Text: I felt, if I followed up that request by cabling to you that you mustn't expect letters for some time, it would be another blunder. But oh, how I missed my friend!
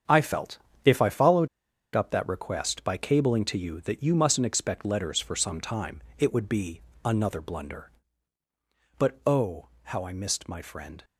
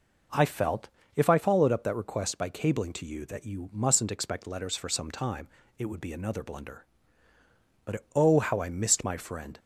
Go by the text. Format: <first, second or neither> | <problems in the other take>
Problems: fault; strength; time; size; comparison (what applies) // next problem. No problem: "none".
second | starts louder than the rest; strong; until 1.3 s; 7.5 dB // pauses between "followed" and "up"; noticeable; at 1.4 s; 0.46 s long // pauses between "be" and "another"; slight; at 6.8 s; 0.24 s long